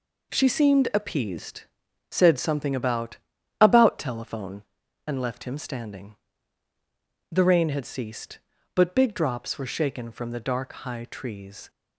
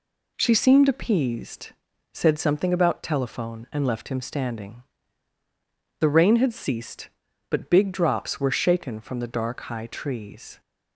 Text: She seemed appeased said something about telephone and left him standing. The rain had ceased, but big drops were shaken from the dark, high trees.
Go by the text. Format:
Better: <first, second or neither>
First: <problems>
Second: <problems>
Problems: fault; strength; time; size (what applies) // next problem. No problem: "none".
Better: second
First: pauses between "appeased" and "said"; noticeable; at 1.6 s; 0.50 s long // says "about" twice; at 3.5 s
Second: pauses between "appeased" and "said"; noticeable; at 1.7 s; 0.46 s long